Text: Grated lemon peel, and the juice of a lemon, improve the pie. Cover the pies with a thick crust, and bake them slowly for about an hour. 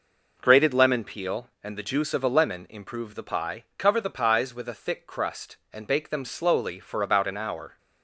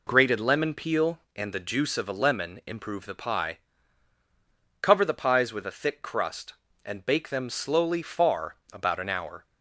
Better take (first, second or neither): first